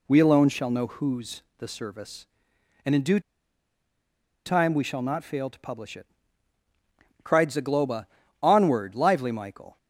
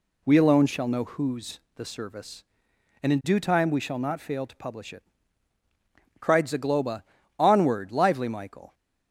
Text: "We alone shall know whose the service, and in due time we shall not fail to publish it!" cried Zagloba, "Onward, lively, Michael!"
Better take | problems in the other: second | pauses between "whose" and "the"; slight; at 1.4 s; 0.16 s long; slight in the second // pauses between "due" and "time"; strong; at 3.1 s; 1.2 s long

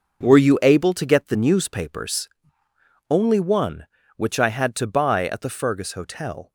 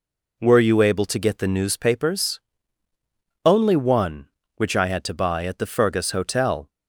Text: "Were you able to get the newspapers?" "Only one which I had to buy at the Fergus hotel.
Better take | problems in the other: second | gets quieter; strong; throughout; 9.5 dB

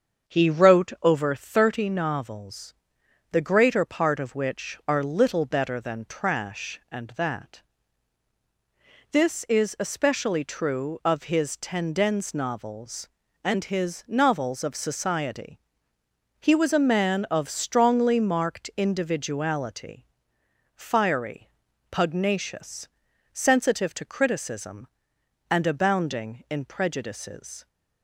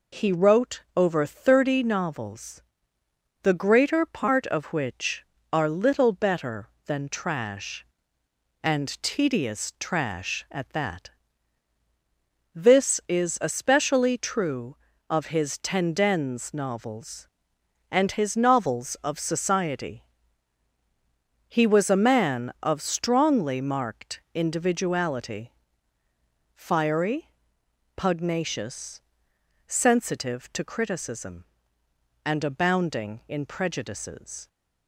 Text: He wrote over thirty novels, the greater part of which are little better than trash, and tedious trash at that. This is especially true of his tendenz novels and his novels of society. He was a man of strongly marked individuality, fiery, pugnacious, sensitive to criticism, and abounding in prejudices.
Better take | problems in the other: second | starts louder than the rest; until 1.3 s; 7 dB // skips "tedious trash at"; at 7.1 s

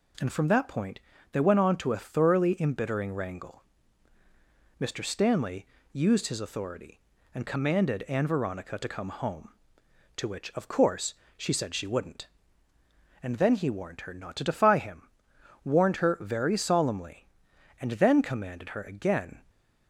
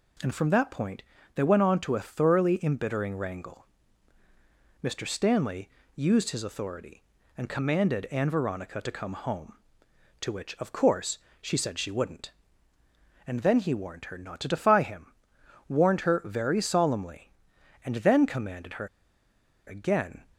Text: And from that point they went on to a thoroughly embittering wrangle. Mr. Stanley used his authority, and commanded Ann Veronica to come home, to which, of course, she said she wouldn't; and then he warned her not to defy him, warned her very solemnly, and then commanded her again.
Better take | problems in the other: first | pauses between "point" and "they"; slight; at 1.0 s; 0.34 s long; slight in the first // pauses between "Stanley" and "used"; slight; at 5.6 s; 0.26 s long; slight in the first // pauses between "her" and "again"; noticeable; at 18.8 s; 0.79 s long

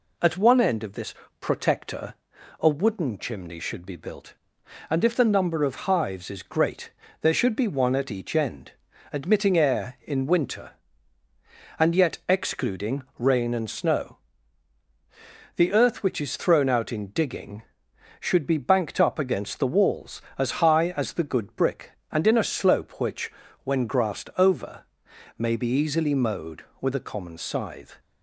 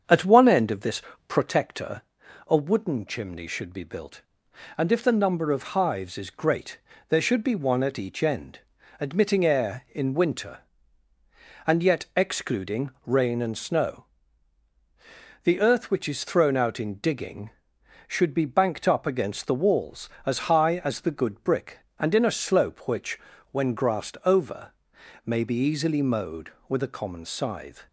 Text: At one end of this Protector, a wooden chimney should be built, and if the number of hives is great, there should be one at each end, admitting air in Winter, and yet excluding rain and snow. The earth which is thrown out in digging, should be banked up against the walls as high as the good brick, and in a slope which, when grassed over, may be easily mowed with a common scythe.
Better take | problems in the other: first | starts louder than the rest; strong; until 1.5 s; 7.5 dB // pauses between "this" and "Protector"; slight; at 1.0 s; 0.28 s long; slight in the first // pauses between "excluding" and "rain"; slight; at 12.9 s; 0.16 s long; slight in the first

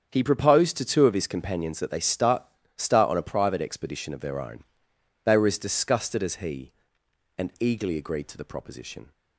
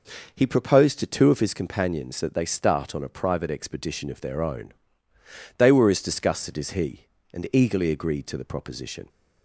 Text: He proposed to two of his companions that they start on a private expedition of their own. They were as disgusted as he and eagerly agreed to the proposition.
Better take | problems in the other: second | starts louder than the rest; strong; until 1.1 s; 8 dB // says "start" twice; at 2.7 s

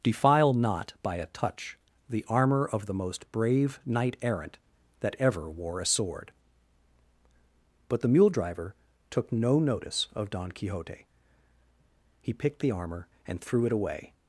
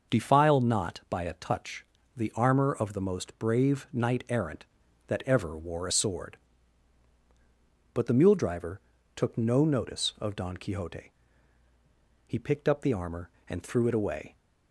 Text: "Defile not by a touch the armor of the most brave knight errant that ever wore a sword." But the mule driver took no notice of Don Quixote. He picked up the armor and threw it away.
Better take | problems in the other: second | starts louder than the rest; noticeable; until 1.1 s; 6 dB; noticeable in the second // pauses between "touch" and "the"; slight; at 1.7 s; 0.32 s long; slight in the second // pauses between "driver" and "took"; at 8.7 s; 0.38 s long; also in the second // skips "up"; at 12.6 s

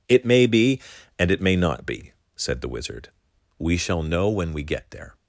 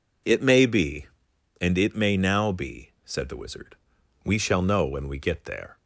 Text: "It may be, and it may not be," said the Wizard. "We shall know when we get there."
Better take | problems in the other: first | says "now" for "not"; at 2.1 s

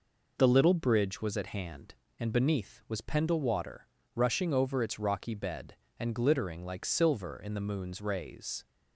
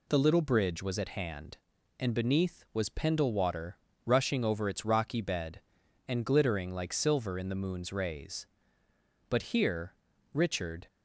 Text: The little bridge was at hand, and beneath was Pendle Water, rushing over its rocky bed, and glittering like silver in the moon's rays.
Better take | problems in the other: first | goes on to say "But here Richard"; from 9.2 s on; 1.5 s long

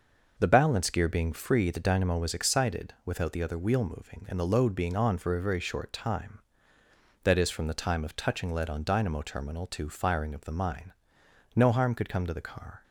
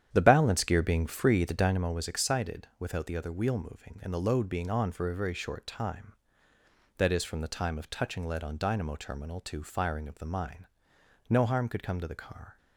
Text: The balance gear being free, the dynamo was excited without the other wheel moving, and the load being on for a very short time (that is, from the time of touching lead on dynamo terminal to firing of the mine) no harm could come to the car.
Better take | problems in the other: first | starts louder than the rest; strong; until 1.9 s; 9.5 dB

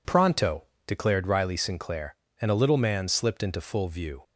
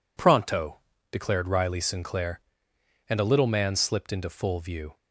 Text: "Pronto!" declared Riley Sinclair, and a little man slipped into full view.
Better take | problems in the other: neither | none

